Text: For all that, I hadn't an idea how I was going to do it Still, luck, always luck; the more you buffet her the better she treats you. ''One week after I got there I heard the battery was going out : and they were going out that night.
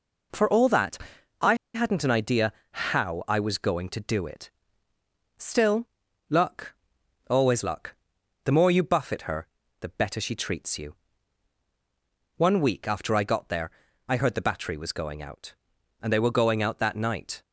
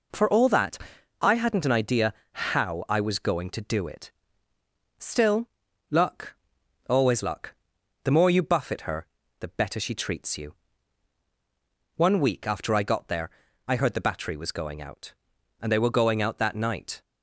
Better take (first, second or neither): second